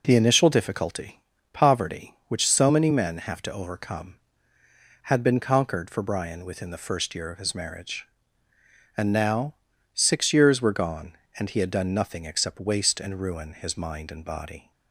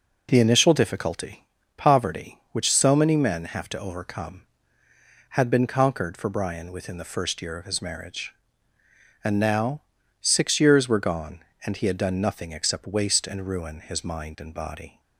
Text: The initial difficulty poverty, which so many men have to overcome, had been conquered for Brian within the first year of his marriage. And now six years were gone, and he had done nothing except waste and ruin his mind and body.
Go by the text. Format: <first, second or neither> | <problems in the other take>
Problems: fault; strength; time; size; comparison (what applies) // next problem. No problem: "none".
neither | pauses between "difficulty" and "poverty"; slight; the same in both // pauses between "now" and "six"; the same in both